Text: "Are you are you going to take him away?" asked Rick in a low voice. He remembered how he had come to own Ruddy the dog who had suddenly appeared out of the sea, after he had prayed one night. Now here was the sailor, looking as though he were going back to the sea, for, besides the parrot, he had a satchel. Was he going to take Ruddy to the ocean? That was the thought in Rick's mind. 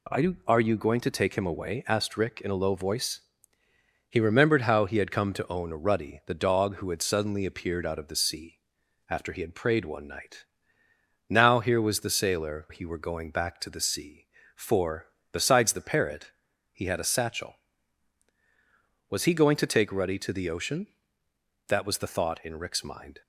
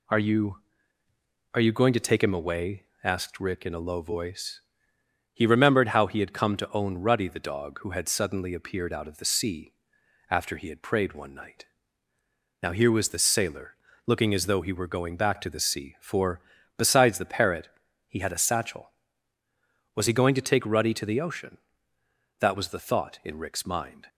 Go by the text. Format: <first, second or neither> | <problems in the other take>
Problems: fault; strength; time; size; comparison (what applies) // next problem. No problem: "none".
second | skips "looking as though"; at 12.6 s